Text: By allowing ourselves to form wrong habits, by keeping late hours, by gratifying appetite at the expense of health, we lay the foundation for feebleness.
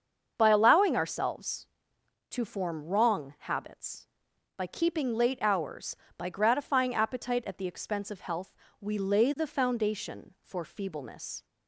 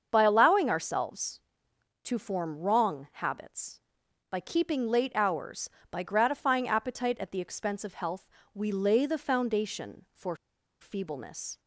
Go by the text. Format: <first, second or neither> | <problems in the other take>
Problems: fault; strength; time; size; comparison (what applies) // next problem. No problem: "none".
first | starts louder than the rest; until 1.1 s; 7 dB; also in the first // pauses between "for" and "feebleness"; at 10.3 s; 0.44 s long